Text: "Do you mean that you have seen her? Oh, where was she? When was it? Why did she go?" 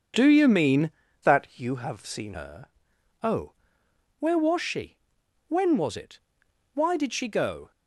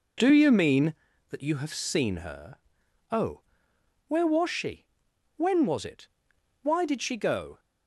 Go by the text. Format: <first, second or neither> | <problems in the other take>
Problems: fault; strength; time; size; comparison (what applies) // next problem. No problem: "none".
second | changes voice from "that" to "seen"; from 1.2 to 2.3 s; 1.1 s long